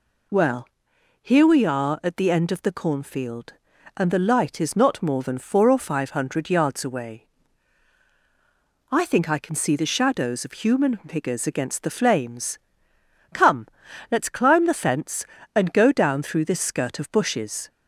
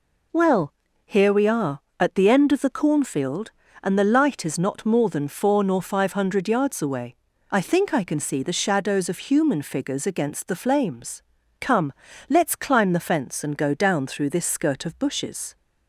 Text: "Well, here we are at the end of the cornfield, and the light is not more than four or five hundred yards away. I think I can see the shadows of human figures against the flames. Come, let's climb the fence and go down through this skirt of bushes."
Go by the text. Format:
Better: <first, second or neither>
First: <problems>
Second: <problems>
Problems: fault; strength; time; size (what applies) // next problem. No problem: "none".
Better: first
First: none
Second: says "nor" for "or"; at 5.6 s